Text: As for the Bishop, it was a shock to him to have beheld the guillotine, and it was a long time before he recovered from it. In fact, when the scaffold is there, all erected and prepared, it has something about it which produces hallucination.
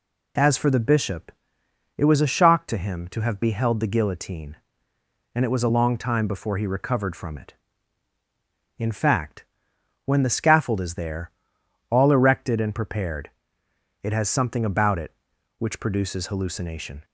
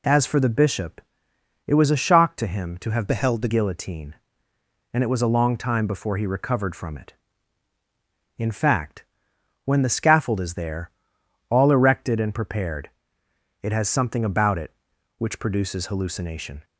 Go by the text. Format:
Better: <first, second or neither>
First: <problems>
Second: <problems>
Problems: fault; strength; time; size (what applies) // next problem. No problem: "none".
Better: first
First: none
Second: changes voice from "beheld" to "the"; from 3.0 to 3.4 s; 0.4 s long